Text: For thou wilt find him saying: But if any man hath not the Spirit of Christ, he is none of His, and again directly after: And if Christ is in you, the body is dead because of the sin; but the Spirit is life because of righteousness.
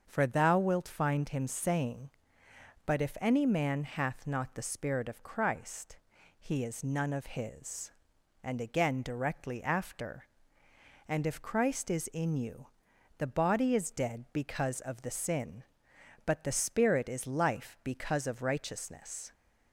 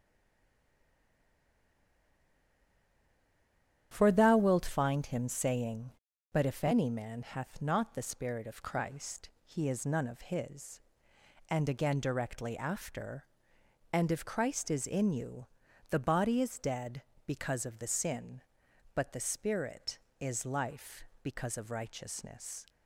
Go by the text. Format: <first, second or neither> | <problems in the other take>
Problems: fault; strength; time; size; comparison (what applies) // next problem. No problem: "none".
first | stays silent before the first word; strong; until 3.9 s; 3.9 s long // starts louder than the rest; strong; until 4.9 s; 10 dB; also in the first